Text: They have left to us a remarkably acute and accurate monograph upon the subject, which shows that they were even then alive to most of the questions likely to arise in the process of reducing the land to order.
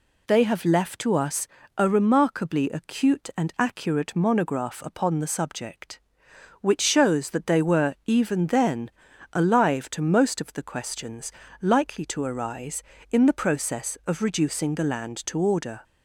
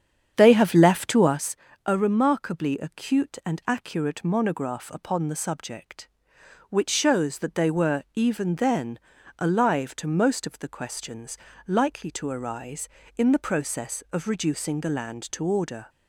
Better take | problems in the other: first | starts louder than the rest; strong; until 1.4 s; 8 dB // pauses between "us" and "a"; slight; at 1.5 s; 0.30 s long; slight in the first // pauses between "then" and "alive"; at 8.9 s; 0.40 s long; also in the first // pauses between "questions" and "likely"; slight; at 11.3 s; 0.30 s long; slight in the first

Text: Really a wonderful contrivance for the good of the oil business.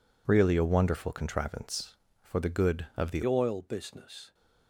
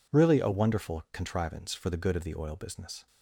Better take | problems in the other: second | changes voice at "oil"; from 3.2 s on; 1.1 s long

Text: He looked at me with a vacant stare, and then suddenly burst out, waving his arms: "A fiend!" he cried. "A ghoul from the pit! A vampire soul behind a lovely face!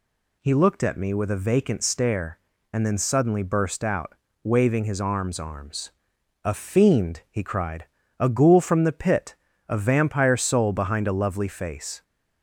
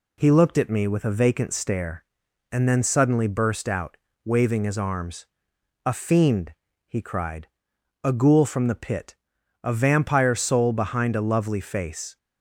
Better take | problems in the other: second | says "arms" twice; at 5.3 s

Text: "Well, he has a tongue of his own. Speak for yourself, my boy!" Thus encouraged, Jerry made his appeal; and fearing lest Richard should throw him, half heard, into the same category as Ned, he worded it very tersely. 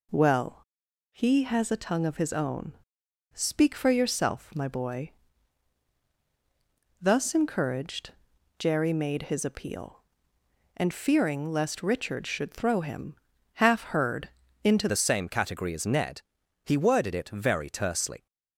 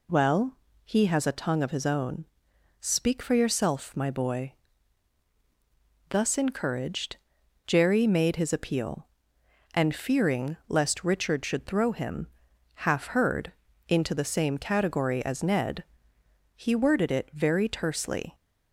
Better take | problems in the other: second | changes voice at "the"; from 14.8 s on; 3.4 s long

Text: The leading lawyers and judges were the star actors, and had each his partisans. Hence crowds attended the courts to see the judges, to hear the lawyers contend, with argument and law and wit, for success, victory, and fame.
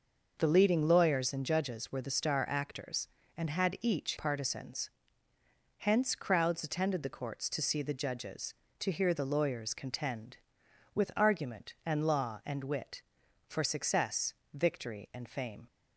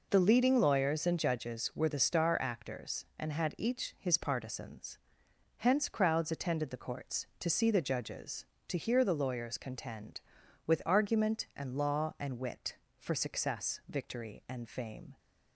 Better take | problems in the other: second | skips "his"; at 4.1 s

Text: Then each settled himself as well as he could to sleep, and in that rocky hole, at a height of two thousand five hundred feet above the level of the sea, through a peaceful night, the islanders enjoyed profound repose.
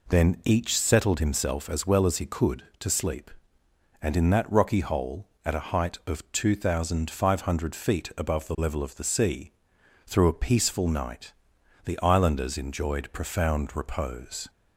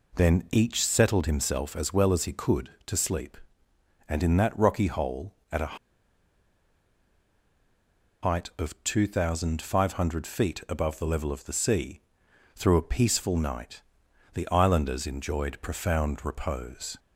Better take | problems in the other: first | pauses between "a" and "height"; strong; at 5.7 s; 2.4 s long

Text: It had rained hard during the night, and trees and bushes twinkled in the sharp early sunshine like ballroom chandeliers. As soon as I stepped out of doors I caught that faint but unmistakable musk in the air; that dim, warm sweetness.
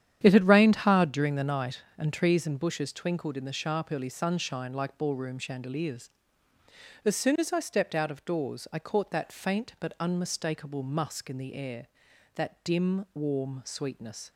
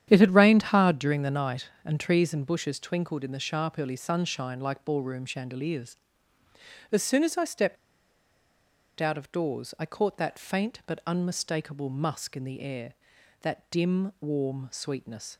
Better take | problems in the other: first | starts louder than the rest; strong; until 1.0 s; 9.5 dB; strong in the first // pauses between "stepped" and "out"; strong; at 7.7 s; 1.2 s long

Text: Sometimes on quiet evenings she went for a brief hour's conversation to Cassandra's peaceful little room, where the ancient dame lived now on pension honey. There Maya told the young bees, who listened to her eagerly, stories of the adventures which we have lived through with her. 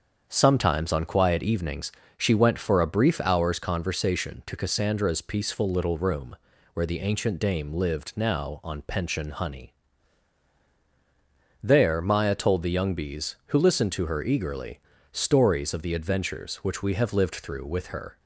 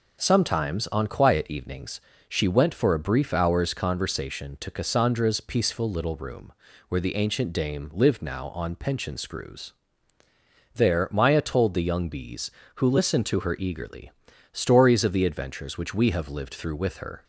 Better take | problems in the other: first | starts louder than the rest; until 1.2 s; 6.5 dB; strong in the first // pauses between "evenings" and "she"; slight; at 2.0 s; 0.26 s long; slight in the first // says "screws" for "honey"; at 9.1 s

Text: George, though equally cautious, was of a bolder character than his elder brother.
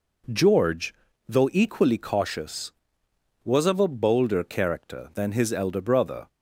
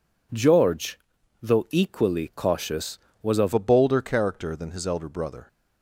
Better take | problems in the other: first | changes voice at "a"; from 3.5 s on; 1.9 s long

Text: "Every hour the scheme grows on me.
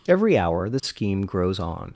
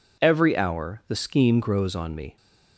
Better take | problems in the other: second | stops before "me"; at 1.9 s

